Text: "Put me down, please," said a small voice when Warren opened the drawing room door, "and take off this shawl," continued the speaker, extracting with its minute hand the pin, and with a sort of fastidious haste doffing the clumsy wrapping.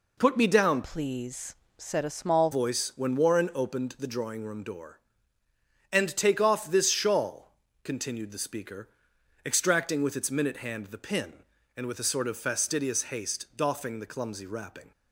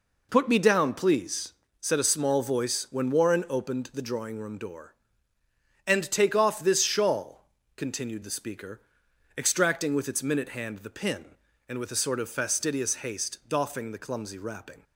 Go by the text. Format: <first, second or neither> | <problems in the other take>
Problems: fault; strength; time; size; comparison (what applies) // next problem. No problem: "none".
second | changes voice from "please" to "small"; from 0.8 to 2.5 s; 1.7 s long